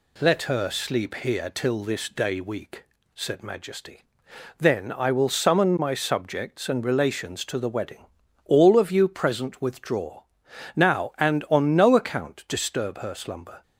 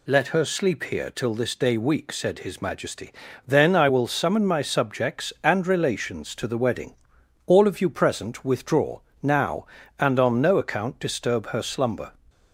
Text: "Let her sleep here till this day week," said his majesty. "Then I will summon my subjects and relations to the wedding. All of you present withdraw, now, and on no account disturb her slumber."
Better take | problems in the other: second | skips "his"; at 3.4 s

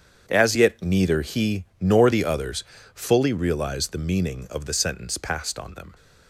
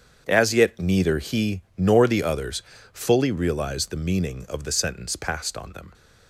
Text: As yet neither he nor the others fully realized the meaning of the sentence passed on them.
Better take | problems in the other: neither | starts louder than the rest; strong; the same in both // pauses between "he" and "nor"; slight; the same in both // pauses between "others" and "fully"; slight; the same in both

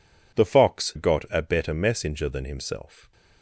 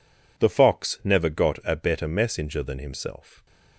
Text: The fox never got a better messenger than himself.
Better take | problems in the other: second | skips "never"; at 0.9 s

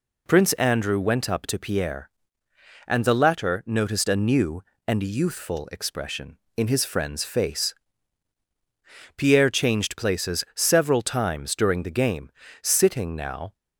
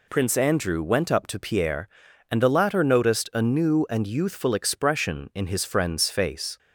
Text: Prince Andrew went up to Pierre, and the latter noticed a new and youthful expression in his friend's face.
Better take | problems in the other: second | goes on to say "Pierre changed places several times during the game sitting now"; strong; from 9.1 s on; 4.3 s long

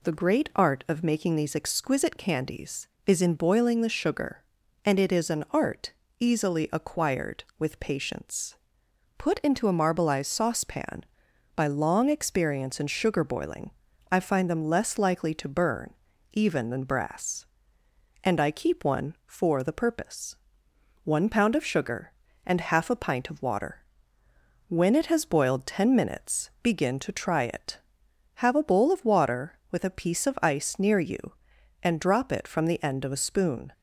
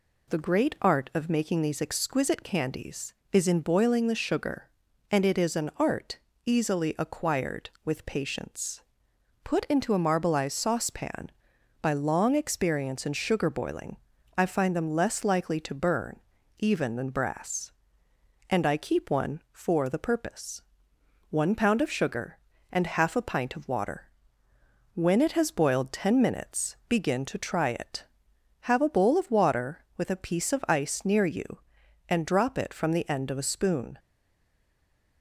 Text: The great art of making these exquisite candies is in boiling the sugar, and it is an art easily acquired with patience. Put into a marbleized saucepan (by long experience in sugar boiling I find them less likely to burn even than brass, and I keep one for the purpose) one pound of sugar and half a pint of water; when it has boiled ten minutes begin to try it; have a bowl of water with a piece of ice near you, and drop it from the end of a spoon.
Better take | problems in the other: first | pauses between "art" and "easily"; slight; at 6.1 s; 0.26 s long; slight in the first // pauses between "boiling" and "I"; at 13.9 s; 0.40 s long; also in the first // pauses between "burn" and "even"; at 16.1 s; 0.38 s long; also in the first // stays silent after the last word; noticeable; from 33.9 s on; 1.3 s long

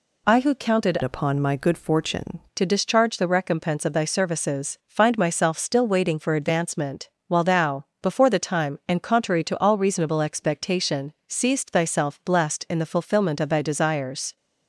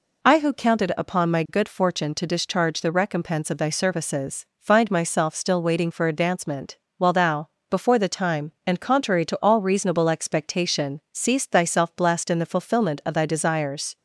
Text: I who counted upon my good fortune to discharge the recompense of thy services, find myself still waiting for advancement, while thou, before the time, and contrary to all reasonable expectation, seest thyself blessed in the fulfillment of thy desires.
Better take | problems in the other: second | changes voice from "upon" to "fortune"; from 1.0 to 2.4 s; 1.4 s long

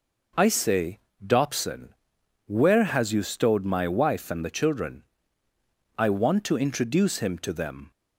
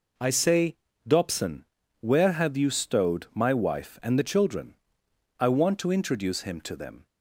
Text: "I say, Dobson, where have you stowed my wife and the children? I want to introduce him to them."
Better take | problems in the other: second | says "has" for "have"; at 2.8 s

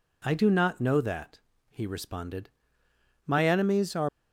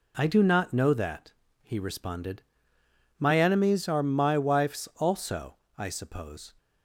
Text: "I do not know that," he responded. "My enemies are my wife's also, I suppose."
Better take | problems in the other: second | stops before "my wife's also I suppose"; at 4.0 s

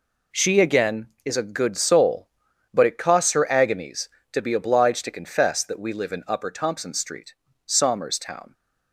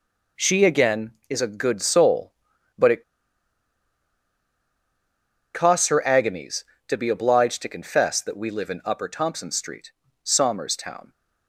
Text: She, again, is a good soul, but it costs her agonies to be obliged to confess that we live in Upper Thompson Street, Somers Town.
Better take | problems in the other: first | pauses between "it" and "costs"; strong; at 3.0 s; 2.5 s long

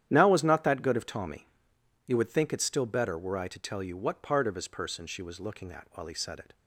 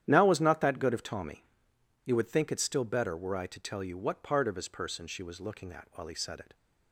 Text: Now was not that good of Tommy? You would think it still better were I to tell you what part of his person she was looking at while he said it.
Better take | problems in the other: neither | starts louder than the rest; strong; the same in both

